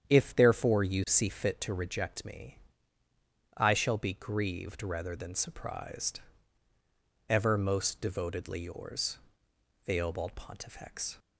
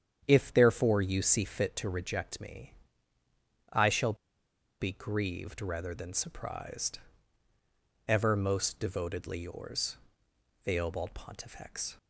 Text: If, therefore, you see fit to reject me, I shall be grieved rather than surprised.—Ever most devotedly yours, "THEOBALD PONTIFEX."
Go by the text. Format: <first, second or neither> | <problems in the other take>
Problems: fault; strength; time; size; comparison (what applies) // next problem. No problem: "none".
first | starts louder than the rest; strong; until 1.2 s; 8.5 dB; strong in the first // pauses between "shall" and "be"; noticeable; at 4.1 s; 0.66 s long